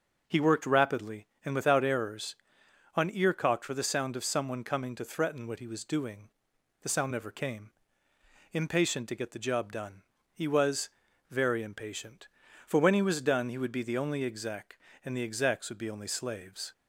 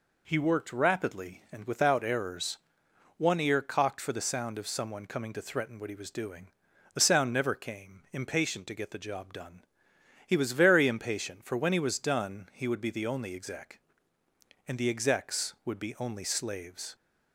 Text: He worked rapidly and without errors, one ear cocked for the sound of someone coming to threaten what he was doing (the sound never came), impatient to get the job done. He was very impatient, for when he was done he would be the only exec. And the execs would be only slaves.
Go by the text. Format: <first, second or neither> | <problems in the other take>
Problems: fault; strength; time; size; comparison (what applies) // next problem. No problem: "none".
second | starts louder than the rest; noticeable; until 1.2 s; 6 dB // says "on" for "one"; at 2.9 s // pauses between "was" and "very"; at 10.8 s; 0.42 s long